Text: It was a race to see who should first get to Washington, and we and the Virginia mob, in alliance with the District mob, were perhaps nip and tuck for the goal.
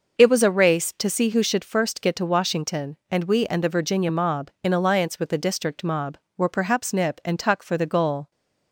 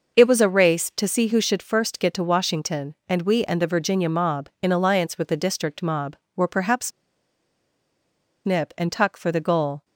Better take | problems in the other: first | pauses between "perhaps" and "nip"; strong; at 6.9 s; 1.5 s long

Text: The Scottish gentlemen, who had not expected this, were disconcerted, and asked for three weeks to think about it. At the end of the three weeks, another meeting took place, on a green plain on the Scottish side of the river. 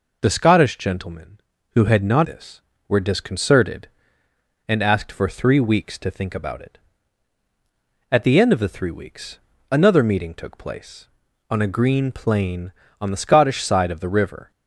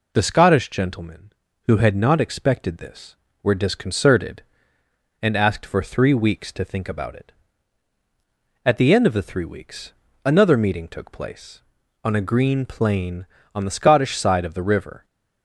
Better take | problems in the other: second | skips "expected"; at 2.2 s

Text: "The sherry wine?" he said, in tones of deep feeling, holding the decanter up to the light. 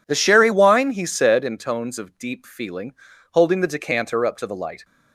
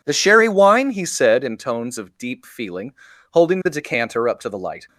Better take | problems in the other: neither | none

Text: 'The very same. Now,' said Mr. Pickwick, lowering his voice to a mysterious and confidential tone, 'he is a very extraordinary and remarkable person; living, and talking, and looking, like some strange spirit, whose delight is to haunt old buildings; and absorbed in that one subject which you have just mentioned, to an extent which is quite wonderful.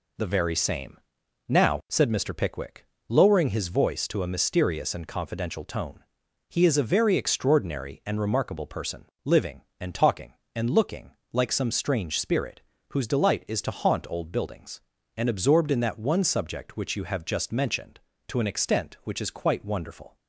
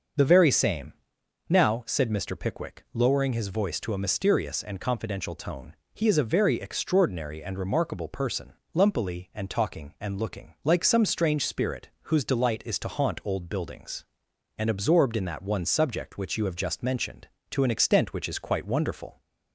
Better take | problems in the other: first | starts louder than the rest; until 1.7 s; 6.5 dB // says "lumpily" for "living"; at 8.7 s

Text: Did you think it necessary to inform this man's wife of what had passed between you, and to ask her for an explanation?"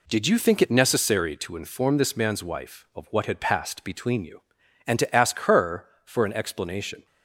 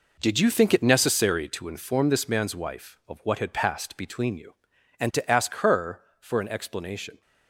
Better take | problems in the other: first | gets quieter; strong; throughout; 11 dB

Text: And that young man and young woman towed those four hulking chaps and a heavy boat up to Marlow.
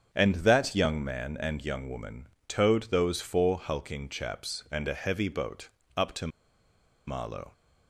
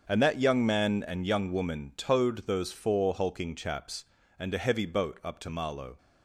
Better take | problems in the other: second | starts louder than the rest; strong; until 1.2 s; 7.5 dB; also in the second // pauses between "woman" and "towed"; slight; at 2.2 s; 0.20 s long // pauses between "boat" and "up"; slight; at 5.6 s; 0.26 s long // pauses between "to" and "Marlow"; noticeable; at 6.2 s; 0.79 s long

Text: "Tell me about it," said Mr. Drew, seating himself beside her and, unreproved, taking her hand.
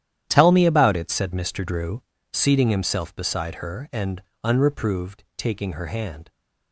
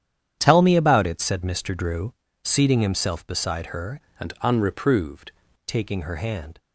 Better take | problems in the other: first | starts louder than the rest; strong; until 1.4 s; 9.5 dB; strong in the first // changes voice from "and" to "unreproved"; from 4.2 to 5.3 s; 1.1 s long

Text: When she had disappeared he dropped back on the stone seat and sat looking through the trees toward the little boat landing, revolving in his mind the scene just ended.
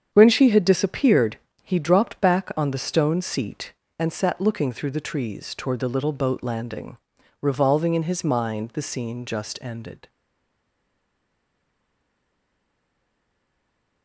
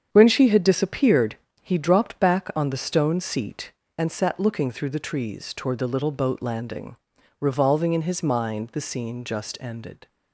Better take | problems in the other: second | starts louder than the rest; strong; until 1.1 s; 8 dB; strong in the second // pauses between "disappeared" and "he"; slight; at 1.3 s; 0.26 s long; slight in the second // stays silent after the last word; strong; from 10.0 s on; 4.0 s long

